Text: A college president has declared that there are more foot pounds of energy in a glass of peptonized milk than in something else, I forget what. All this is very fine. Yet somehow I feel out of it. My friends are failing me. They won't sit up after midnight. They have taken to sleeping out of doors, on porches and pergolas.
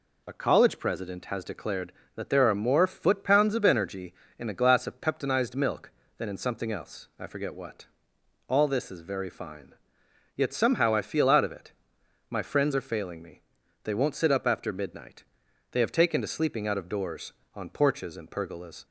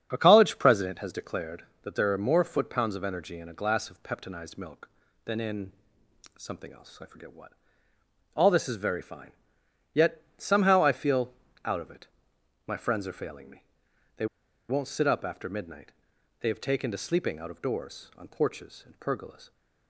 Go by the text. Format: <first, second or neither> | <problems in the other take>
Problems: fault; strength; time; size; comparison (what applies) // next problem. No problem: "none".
first | starts louder than the rest; strong; until 1.1 s; 7.5 dB // pauses between "in" and "something"; noticeable; at 5.7 s; 0.66 s long // pauses between "Yet" and "somehow"; slight; at 10.2 s; 0.16 s long // pauses between "feel" and "out"; slight; at 11.3 s; 0.32 s long // pauses between "They" and "won't"; at 14.2 s; 0.43 s long